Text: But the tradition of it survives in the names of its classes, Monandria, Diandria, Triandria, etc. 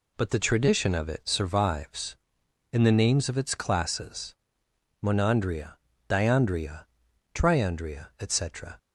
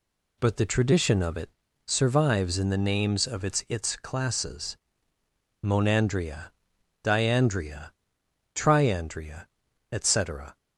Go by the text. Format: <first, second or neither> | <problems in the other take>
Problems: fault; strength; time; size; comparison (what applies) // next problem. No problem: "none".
first | pauses between "it" and "survives"; at 1.4 s; 0.38 s long // says "its" twice; at 3.6 s